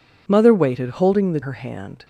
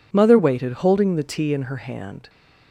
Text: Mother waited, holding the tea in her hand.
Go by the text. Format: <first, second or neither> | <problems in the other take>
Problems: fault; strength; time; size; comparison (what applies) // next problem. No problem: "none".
second | skips "tea in"; at 1.4 s